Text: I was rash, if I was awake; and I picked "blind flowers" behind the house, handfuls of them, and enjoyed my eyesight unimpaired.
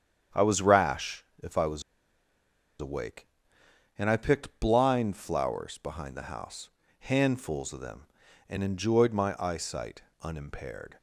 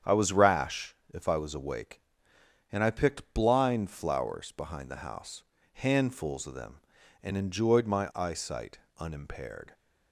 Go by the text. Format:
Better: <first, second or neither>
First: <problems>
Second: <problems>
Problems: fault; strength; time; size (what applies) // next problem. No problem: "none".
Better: second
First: starts louder than the rest; strong; until 1.5 s; 8 dB // pauses between "was" and "awake"; at 1.8 s; 0.98 s long // pauses between "eyesight" and "unimpaired"; slight; at 10.0 s; 0.22 s long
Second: starts louder than the rest; strong; until 1.2 s; 8 dB // pauses between "eyesight" and "unimpaired"; slight; at 8.7 s; 0.22 s long